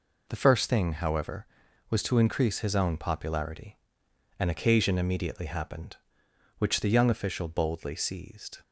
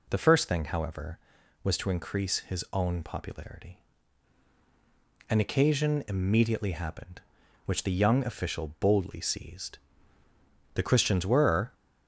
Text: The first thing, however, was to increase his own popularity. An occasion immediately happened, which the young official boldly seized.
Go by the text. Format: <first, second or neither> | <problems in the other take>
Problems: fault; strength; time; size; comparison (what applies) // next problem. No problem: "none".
first | goes on to say "The Christians were"; noticeable; from 10.7 s on; 0.98 s long